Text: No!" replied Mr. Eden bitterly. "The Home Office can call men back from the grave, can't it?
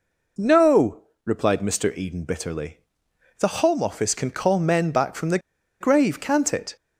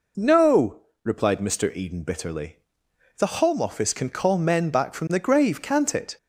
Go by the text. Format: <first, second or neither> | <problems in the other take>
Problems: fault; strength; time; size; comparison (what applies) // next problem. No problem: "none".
second | pauses between "the" and "grave"; at 5.3 s; 0.42 s long